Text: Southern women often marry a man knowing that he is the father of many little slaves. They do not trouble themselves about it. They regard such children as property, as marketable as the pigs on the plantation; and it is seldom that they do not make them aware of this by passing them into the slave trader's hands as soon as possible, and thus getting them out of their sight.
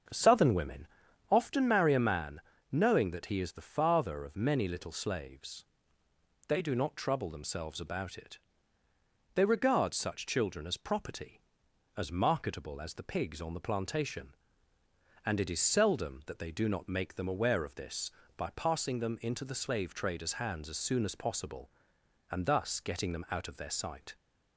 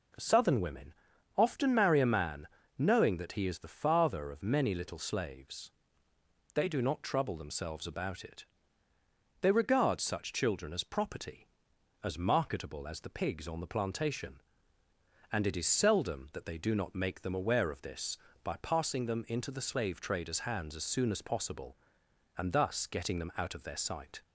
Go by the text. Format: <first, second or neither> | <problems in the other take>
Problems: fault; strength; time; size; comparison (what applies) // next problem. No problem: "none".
second | starts louder than the rest; until 1.4 s; 7 dB // pauses between "women" and "often"; at 0.8 s; 0.42 s long; also in the second // pauses between "man" and "knowing"; slight; at 2.3 s; 0.32 s long; slight in the second